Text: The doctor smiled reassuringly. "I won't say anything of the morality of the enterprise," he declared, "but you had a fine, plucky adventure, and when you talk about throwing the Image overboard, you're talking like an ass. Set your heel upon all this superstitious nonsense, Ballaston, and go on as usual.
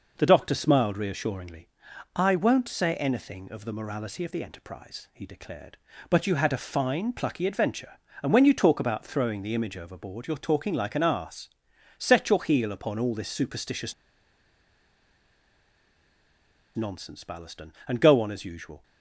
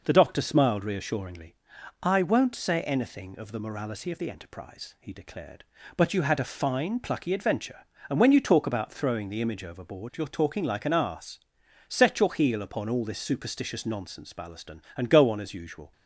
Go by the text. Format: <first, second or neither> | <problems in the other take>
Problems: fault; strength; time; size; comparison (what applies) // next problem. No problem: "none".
second | pauses between "superstitious" and "nonsense"; strong; at 13.9 s; 2.8 s long